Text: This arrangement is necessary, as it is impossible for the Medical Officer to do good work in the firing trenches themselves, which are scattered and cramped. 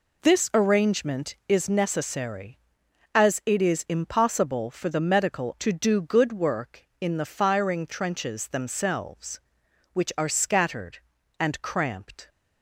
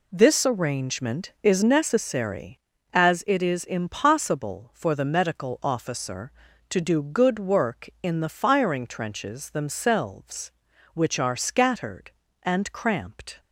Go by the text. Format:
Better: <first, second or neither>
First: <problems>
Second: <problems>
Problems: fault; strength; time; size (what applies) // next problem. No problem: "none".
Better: second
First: skips "Officer"; at 5.5 s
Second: none